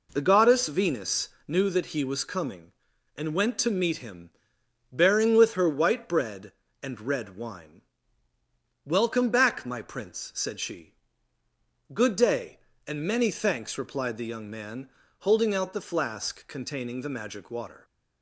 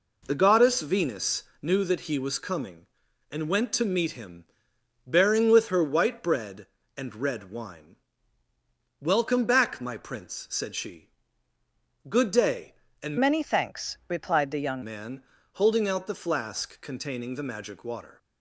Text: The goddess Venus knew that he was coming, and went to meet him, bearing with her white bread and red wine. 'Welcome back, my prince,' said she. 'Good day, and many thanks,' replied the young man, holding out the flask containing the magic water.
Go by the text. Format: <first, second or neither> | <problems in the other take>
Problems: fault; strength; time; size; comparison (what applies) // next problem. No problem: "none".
first | pauses between "Venus" and "knew"; slight; at 1.4 s; 0.18 s long; slight in the first // changes voice from "many" to "young"; from 13.1 to 14.8 s; 1.7 s long